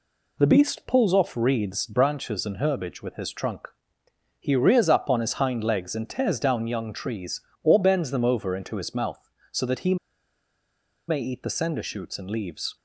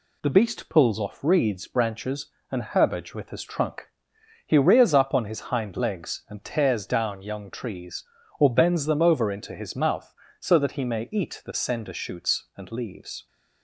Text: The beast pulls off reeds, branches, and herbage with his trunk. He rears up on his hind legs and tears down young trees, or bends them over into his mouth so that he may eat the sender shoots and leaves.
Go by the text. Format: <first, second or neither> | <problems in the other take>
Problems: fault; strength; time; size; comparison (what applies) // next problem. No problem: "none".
second | pauses between "he" and "may"; at 9.9 s; 1.1 s long